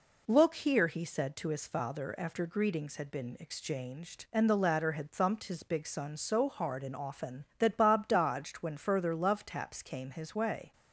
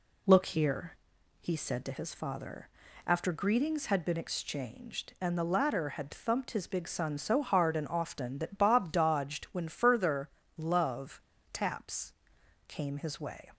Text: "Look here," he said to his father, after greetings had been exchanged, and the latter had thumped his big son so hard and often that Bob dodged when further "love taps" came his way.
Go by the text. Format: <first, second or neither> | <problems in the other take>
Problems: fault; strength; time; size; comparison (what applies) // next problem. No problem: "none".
first | pauses between "further" and "love"; slight; at 10.2 s; 0.26 s long // pauses between "love" and "taps"; slight; at 11.1 s; 0.34 s long // pauses between "taps" and "came"; noticeable; at 12.1 s; 0.56 s long